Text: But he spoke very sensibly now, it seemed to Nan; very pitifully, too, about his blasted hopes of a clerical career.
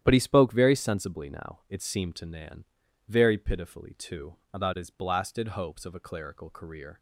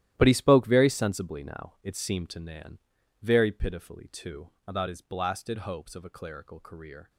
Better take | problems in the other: first | gets quieter; strong; throughout; 14.5 dB // starts louder than the rest; strong; until 1.1 s; 13 dB; strong in the first

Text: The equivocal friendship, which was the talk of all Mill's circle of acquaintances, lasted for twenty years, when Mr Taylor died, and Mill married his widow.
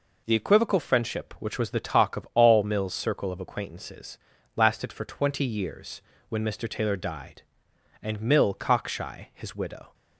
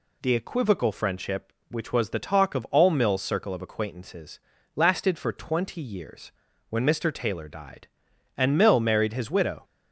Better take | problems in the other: second | says "cockshy" for "married"; at 8.5 s

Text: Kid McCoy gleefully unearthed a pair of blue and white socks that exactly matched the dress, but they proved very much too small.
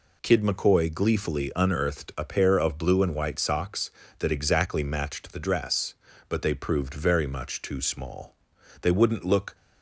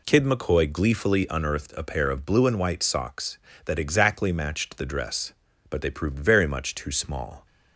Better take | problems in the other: second | goes on to say "They wouldn't look"; noticeable; from 8.8 s on; 0.74 s long

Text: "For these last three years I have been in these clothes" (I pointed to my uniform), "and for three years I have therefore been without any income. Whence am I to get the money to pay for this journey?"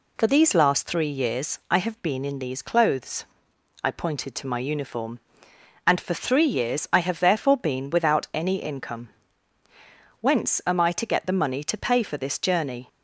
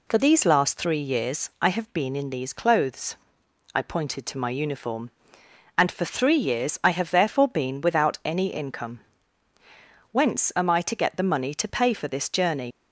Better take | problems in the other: first | leaves "journey" unfinished; at 12.7 s; 75 ms

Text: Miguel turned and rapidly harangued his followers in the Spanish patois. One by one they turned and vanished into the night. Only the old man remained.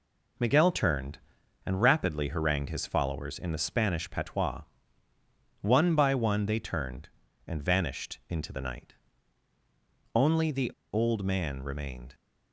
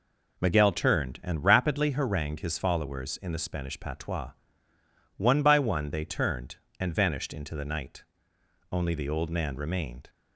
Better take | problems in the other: second | pauses between "the" and "old"; slight; at 10.7 s; 0.22 s long

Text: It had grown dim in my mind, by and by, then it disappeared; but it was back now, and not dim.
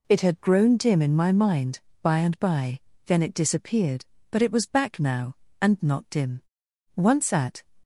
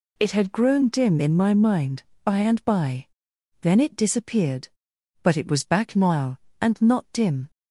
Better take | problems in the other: second | goes on to say "Once at"; noticeable; from 6.9 s on; 0.70 s long

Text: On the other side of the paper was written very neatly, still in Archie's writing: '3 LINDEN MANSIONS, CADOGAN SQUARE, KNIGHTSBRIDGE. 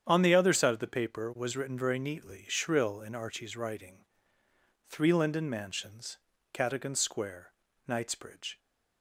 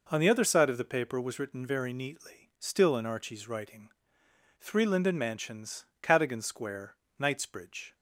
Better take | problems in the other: second | starts louder than the rest; strong; until 1.0 s; 8.5 dB // says "shrill" for "still"; at 2.4 s

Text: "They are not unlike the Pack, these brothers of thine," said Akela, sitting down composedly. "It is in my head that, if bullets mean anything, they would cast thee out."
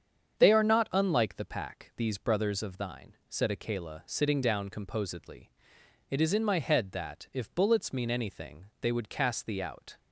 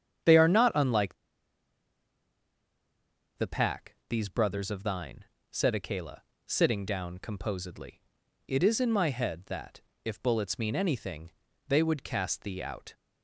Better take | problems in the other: first | starts louder than the rest; strong; until 3.5 s; 8.5 dB; strong in the first // pauses between "unlike" and "the"; strong; at 1.1 s; 2.2 s long

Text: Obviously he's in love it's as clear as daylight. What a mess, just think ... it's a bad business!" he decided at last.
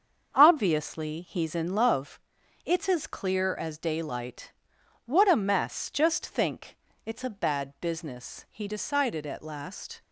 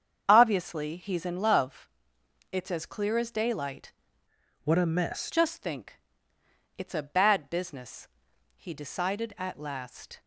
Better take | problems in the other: first | starts louder than the rest; strong; until 1.2 s; 7.5 dB; also in the first // pauses between "love" and "it's"; noticeable; at 1.8 s; 0.62 s long; noticeable in the first // changes voice from "What" to "mess"; from 4.6 to 5.2 s; 0.6 s long

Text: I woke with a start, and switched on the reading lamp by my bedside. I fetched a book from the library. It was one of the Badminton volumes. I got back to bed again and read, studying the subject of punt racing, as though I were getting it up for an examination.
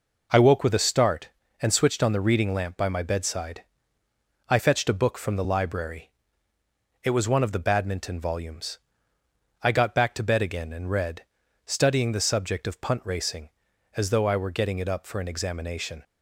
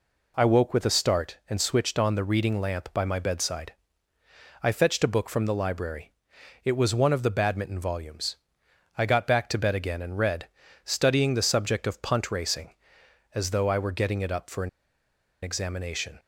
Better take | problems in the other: first | pauses between "an" and "examination"; noticeable; at 14.6 s; 0.74 s long

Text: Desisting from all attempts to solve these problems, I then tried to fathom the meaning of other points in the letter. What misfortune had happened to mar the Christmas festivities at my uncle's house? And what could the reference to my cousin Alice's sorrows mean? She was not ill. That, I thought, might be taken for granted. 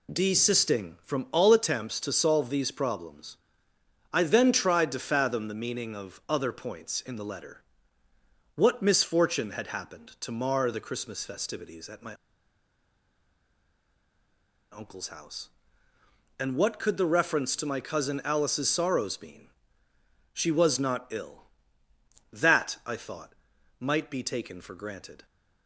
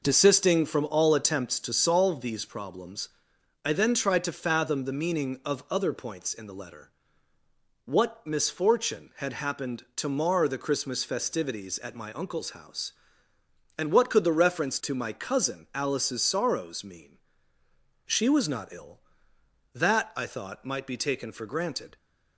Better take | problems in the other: second | pauses between "my" and "uncle's"; strong; at 12.1 s; 2.5 s long

